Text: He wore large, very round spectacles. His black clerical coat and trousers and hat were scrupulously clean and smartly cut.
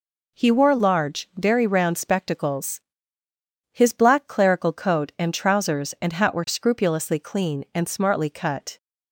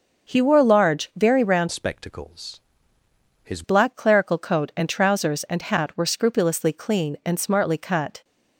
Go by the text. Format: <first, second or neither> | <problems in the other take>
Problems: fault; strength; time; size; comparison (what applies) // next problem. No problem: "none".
first | starts louder than the rest; noticeable; until 1.3 s; 6 dB // changes voice from "spectacles" to "His"; from 1.7 to 3.6 s; 1.9 s long